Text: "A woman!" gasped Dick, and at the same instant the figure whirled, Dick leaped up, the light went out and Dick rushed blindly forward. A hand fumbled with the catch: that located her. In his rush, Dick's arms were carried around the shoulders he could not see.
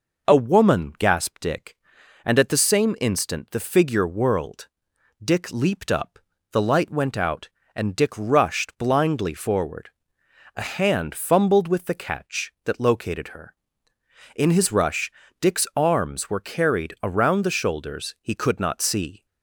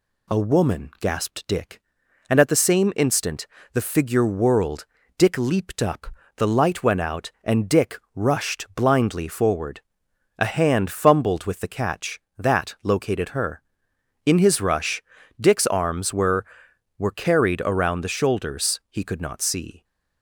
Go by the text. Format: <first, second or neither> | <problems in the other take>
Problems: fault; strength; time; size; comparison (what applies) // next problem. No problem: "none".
first | pauses between "instant" and "the"; slight; at 3.4 s; 0.26 s long // pauses between "Dick" and "rushed"; slight; at 7.9 s; 0.16 s long // says "were" twice; at 16.9 s